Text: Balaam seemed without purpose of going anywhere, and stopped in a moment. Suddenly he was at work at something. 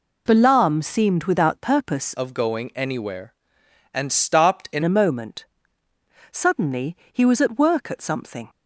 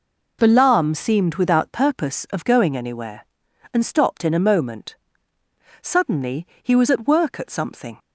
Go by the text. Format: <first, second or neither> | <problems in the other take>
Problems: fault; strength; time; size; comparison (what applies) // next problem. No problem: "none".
second | changes voice from "of" to "in"; from 2.1 to 4.8 s; 2.7 s long // pauses between "Suddenly" and "he"; slight; at 6.9 s; 0.16 s long; slight in the second